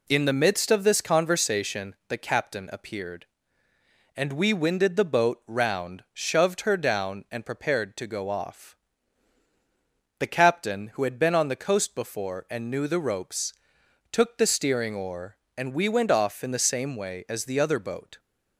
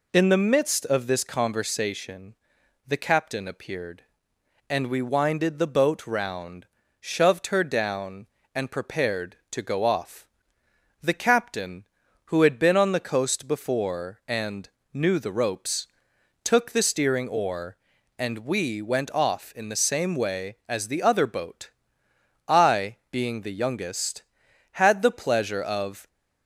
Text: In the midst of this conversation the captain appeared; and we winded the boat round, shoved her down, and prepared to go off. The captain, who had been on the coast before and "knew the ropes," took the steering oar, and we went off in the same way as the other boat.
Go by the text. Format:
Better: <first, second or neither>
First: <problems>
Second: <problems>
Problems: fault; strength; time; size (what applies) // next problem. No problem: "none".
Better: first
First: none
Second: pauses between "conversation" and "the"; noticeable; at 2.3 s; 0.54 s long // pauses between "and" and "knew"; slight; at 14.6 s; 0.24 s long // goes on to say "I being the youngest had the pleasure of"; strong; from 22.4 s on; 3.6 s long